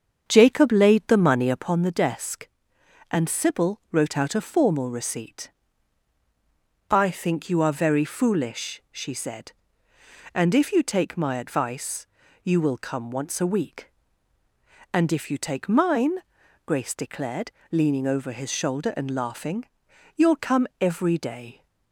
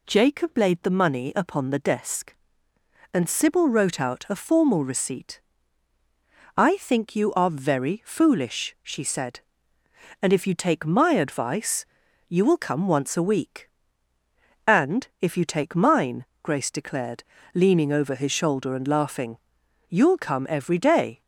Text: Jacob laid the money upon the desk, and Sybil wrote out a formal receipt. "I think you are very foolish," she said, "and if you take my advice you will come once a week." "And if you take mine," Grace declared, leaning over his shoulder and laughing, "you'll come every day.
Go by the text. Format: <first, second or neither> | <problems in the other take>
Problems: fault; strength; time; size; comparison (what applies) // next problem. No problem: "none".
second | starts louder than the rest; strong; until 1.8 s; 7 dB // pauses between "advice" and "you"; slight; at 12.0 s; 0.36 s long; also in the second